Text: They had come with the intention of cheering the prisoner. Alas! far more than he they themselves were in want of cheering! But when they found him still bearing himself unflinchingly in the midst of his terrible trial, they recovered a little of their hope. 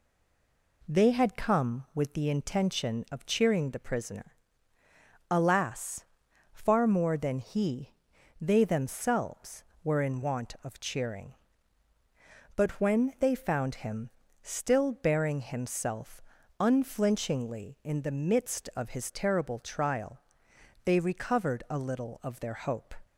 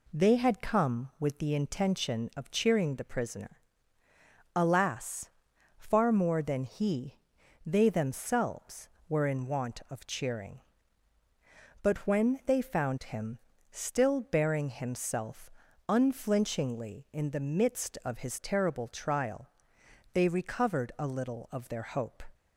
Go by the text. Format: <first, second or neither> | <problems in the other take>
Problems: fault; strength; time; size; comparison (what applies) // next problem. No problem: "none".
second | stays silent before the first word; slight; until 0.8 s; 0.8 s long // pauses between "he" and "they"; noticeable; at 7.9 s; 0.50 s long; noticeable in the second // pauses between "him" and "still"; slight; at 14.0 s; 0.34 s long; slight in the second // pauses between "himself" and "unflinchingly"; slight; at 16.2 s; 0.36 s long; slight in the second